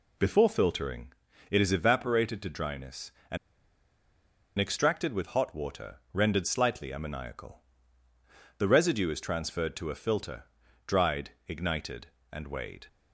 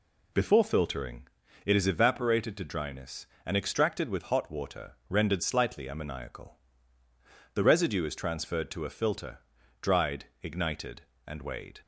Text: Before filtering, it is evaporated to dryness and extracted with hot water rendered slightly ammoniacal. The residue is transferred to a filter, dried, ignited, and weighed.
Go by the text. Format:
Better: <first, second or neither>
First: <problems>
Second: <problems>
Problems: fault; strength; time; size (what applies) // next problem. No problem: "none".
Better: second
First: pauses between "and" and "extracted"; at 3.3 s; 1.2 s long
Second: none